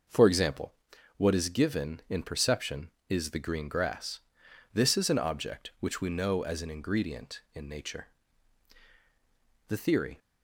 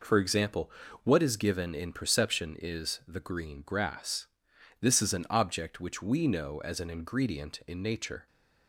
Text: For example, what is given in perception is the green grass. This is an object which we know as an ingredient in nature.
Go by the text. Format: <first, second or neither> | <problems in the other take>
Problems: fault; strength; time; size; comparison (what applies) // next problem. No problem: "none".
second | goes on to say "The theory"; from 9.6 s on; 0.50 s long